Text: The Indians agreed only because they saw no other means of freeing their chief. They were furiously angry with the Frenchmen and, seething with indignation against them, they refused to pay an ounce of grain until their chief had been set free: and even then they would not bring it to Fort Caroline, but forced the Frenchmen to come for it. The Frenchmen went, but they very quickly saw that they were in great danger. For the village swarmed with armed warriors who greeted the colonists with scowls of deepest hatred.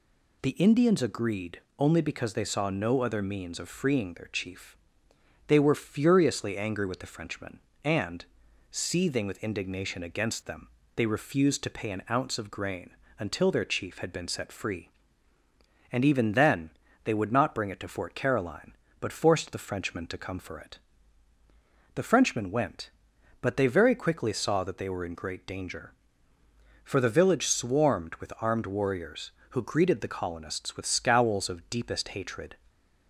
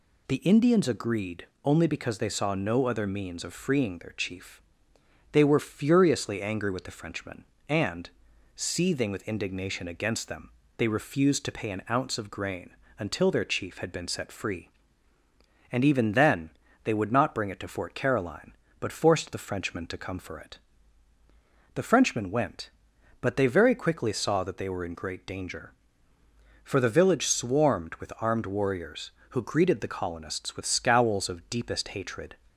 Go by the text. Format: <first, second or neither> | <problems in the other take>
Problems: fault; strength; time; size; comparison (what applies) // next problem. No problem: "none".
neither | pauses between "agreed" and "only"; slight; the same in both // pauses between "grain" and "until"; slight; the same in both // pauses between "then" and "they"; slight; the same in both